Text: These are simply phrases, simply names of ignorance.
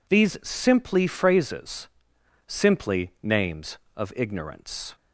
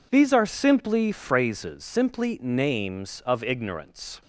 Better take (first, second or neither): second